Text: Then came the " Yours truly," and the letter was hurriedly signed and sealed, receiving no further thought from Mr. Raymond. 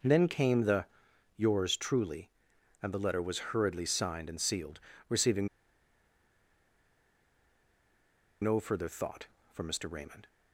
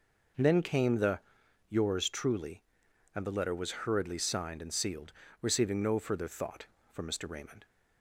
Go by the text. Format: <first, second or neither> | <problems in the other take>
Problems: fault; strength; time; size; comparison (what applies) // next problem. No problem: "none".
second | pauses between "receiving" and "no"; strong; at 5.4 s; 2.9 s long